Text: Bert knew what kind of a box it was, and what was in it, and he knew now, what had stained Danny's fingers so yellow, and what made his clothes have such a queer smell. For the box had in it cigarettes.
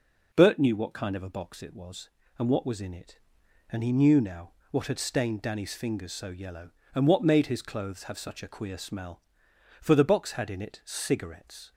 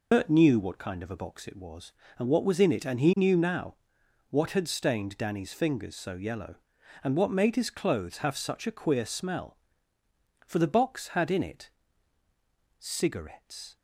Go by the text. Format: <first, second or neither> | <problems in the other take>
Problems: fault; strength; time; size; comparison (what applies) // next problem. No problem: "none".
first | loses the start of "Bert"; at 0.1 s; 85 ms // pauses between "it" and "cigarettes"; at 11.6 s; 1.0 s long